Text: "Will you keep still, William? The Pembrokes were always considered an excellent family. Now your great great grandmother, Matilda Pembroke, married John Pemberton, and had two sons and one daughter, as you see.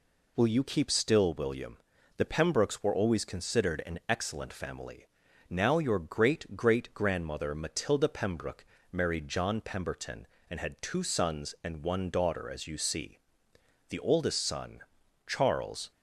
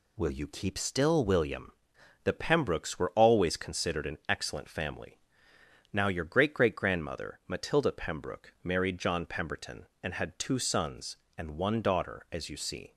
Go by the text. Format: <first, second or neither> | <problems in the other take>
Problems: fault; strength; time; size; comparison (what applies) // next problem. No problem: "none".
second | goes on to say "The oldest son Charles"; strong; from 13.8 s on; 2.0 s long